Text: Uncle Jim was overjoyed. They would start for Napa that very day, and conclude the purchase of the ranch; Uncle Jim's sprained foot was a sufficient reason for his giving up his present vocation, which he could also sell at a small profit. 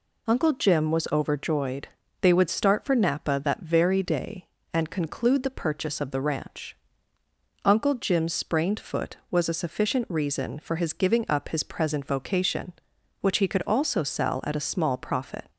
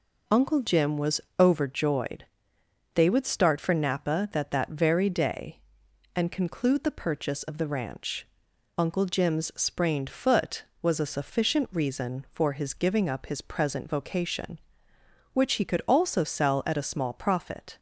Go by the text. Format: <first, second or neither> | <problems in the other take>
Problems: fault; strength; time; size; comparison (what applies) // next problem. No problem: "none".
first | pauses between "was" and "overjoyed"; slight; at 1.2 s; 0.18 s long // says "that" twice; at 4.5 s